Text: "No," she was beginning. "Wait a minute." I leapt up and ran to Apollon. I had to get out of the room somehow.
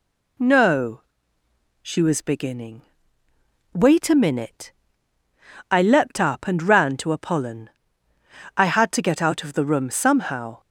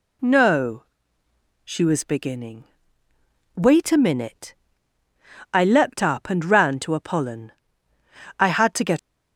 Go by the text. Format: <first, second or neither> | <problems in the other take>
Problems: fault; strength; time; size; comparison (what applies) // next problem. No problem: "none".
first | stops before "out of the room somehow"; at 8.9 s